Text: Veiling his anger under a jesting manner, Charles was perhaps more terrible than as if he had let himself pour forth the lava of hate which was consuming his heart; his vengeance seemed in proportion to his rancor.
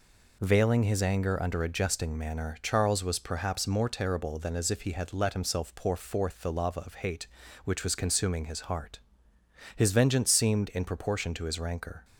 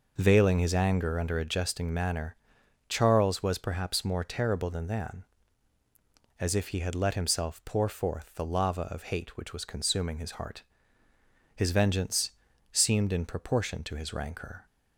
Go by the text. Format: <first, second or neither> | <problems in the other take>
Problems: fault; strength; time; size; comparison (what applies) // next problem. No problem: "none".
first | says "than" twice; at 4.8 s // pauses between "vengeance" and "seemed"; at 12.3 s; 0.40 s long